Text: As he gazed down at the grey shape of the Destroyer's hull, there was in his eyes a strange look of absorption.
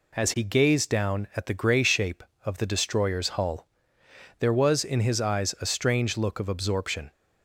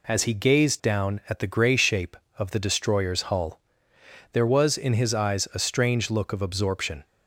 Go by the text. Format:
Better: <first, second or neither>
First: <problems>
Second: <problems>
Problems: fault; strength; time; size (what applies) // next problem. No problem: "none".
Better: neither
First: none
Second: none